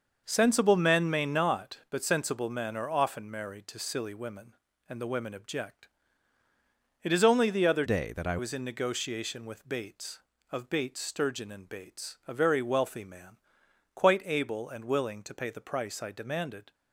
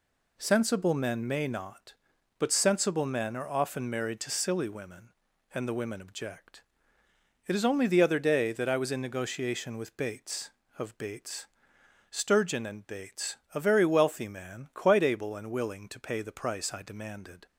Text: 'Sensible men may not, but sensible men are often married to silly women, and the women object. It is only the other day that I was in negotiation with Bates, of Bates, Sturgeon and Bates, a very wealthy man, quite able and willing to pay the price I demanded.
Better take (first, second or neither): second